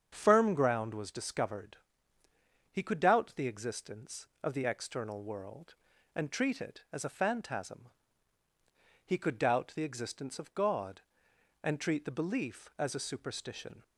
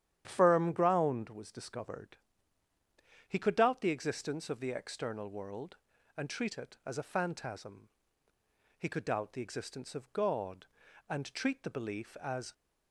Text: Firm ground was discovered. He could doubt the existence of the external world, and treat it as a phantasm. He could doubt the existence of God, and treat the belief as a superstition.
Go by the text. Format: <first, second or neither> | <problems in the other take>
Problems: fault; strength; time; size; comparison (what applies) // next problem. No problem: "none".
first | starts louder than the rest; strong; until 1.2 s; 10.5 dB; strong in the first // stops before "a superstition"; at 12.5 s